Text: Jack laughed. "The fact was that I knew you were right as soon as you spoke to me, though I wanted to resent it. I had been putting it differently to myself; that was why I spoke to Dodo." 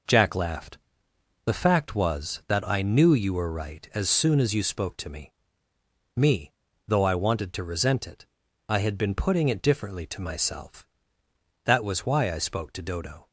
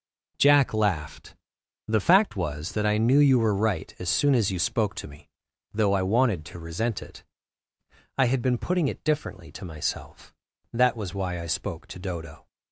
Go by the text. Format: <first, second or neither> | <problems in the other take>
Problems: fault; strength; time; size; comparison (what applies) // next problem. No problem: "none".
second | says "me" twice; at 6.1 s